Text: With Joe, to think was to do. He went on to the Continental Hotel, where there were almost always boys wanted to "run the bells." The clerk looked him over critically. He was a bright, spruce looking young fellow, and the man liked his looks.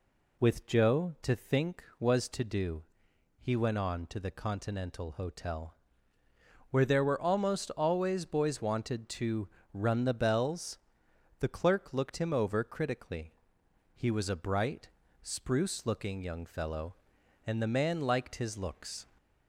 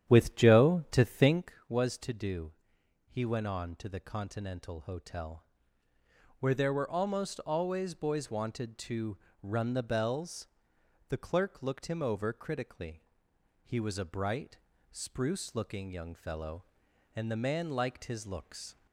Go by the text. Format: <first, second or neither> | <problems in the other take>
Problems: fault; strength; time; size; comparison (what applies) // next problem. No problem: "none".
first | starts louder than the rest; strong; until 1.6 s; 10 dB // pauses between "to" and "run"; slight; at 9.1 s; 0.24 s long; slight in the first